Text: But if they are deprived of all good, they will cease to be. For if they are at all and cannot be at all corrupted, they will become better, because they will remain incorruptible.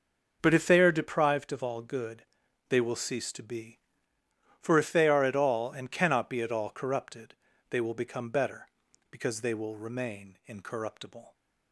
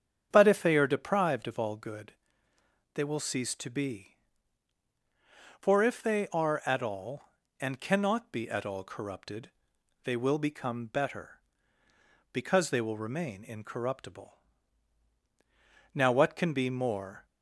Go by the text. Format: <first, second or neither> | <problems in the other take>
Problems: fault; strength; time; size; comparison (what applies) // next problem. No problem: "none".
first | starts louder than the rest; strong; until 1.3 s; 8 dB // goes on to say "Now what can be more"; from 15.9 s on; 1.3 s long